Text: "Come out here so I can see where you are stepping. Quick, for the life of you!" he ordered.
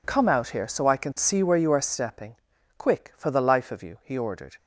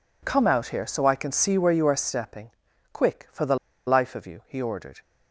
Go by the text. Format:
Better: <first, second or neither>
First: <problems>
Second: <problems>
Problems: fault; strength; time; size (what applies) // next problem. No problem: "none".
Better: first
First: none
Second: pauses between "the" and "life"; slight; at 3.5 s; 0.30 s long